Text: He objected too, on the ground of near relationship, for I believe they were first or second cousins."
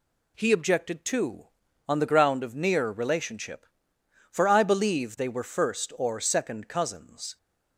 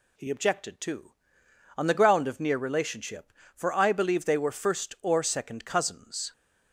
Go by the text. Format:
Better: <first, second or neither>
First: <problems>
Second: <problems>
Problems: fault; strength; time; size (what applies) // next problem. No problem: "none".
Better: neither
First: none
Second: none